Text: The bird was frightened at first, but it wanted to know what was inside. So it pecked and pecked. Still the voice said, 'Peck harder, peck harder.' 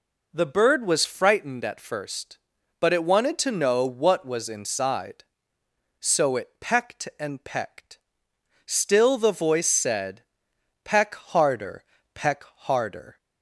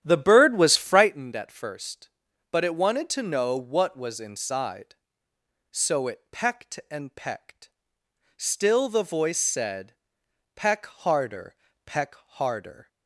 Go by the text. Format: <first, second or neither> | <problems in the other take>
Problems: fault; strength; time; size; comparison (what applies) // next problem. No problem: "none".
first | starts louder than the rest; strong; until 1.2 s; 11 dB